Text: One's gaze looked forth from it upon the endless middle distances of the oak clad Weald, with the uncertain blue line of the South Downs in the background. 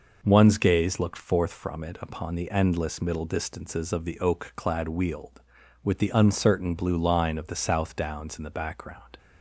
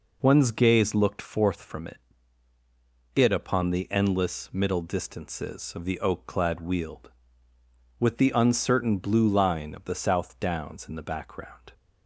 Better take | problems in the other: first | says "it" twice; at 3.1 s

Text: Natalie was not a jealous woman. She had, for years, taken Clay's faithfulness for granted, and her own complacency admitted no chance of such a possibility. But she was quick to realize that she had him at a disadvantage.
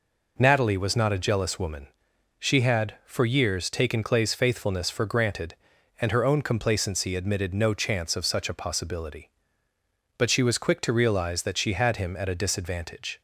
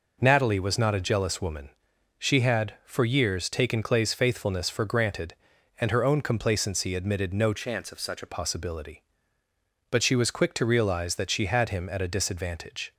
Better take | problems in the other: first | changes voice from "chance" to "a"; from 7.5 to 8.2 s; 0.7 s long

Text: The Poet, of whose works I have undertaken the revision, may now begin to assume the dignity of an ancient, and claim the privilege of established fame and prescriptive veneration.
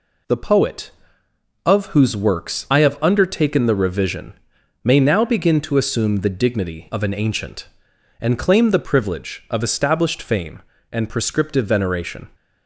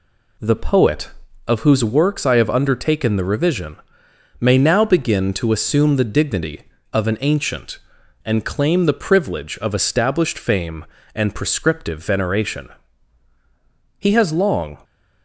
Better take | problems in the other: first | goes on to say "He has long"; noticeable; from 13.9 s on; 0.78 s long

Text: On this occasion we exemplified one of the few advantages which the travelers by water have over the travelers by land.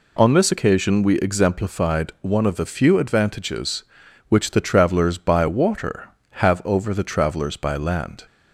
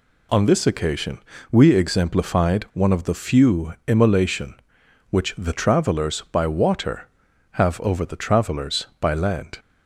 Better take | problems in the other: first | pauses between "occasion" and "we"; slight; at 1.1 s; 0.32 s long // says "immolation" for "advantages"; at 3.8 s

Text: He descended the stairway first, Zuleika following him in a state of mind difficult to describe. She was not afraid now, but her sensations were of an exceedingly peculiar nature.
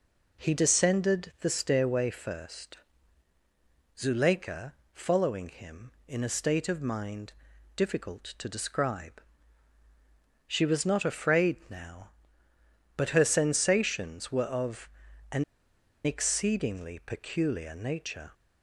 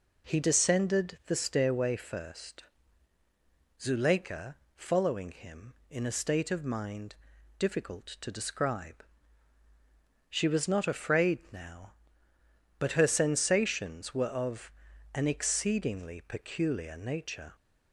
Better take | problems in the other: second | pauses between "Zuleika" and "following"; slight; at 4.7 s; 0.22 s long; slight in the second // pauses between "mind" and "difficult"; at 7.3 s; 0.42 s long; also in the second // pauses between "of" and "an"; at 14.8 s; 0.42 s long; also in the second // pauses between "an" and "exceedingly"; noticeable; at 15.4 s; 0.61 s long

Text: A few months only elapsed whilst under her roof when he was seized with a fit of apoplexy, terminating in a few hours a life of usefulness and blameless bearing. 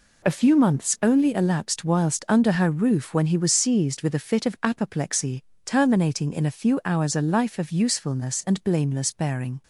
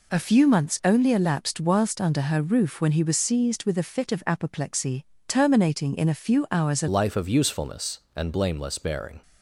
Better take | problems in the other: first | changes voice at "life"; from 6.8 s on; 2.4 s long

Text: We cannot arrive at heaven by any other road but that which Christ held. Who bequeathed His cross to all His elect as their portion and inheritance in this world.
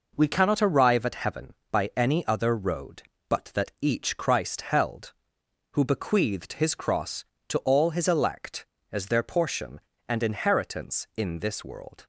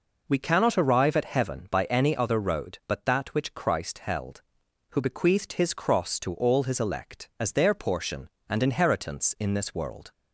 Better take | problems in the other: second | says "each" for "which"; at 3.8 s

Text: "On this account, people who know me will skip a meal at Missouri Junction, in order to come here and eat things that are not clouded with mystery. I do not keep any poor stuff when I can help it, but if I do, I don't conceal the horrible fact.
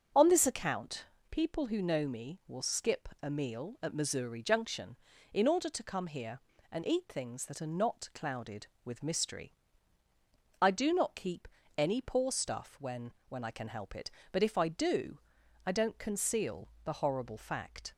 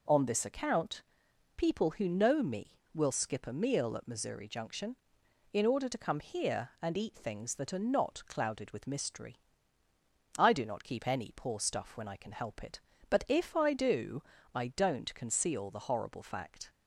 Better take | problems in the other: second | starts louder than the rest; until 1.3 s; 6.5 dB // pauses between "keep" and "any"; slight; at 11.4 s; 0.30 s long // says "when" twice; at 13.2 s // pauses between "conceal" and "the"; slight; at 16.6 s; 0.16 s long

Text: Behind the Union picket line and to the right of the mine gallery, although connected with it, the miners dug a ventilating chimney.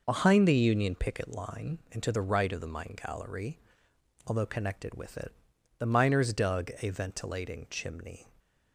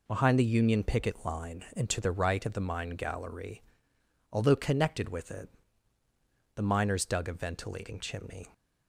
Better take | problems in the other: neither | none

